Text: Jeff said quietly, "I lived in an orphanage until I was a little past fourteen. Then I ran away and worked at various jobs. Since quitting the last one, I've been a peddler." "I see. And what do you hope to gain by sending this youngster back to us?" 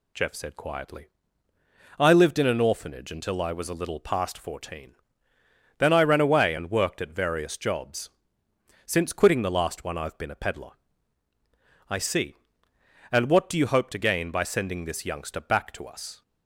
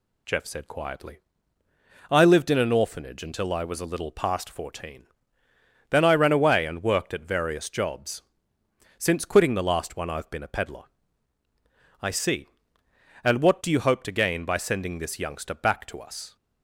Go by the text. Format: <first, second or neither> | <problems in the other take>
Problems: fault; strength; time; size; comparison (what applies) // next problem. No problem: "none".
neither | none